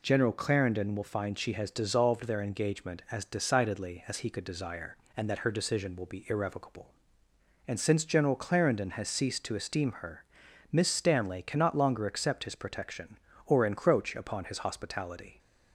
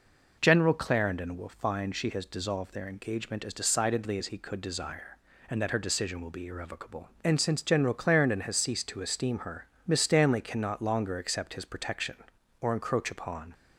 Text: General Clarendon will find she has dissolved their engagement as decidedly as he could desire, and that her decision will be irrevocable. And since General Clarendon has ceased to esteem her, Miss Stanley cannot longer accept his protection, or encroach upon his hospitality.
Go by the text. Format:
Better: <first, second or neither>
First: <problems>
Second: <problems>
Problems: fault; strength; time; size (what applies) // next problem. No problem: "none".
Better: first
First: none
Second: stops before "his hospitality"; at 13.5 s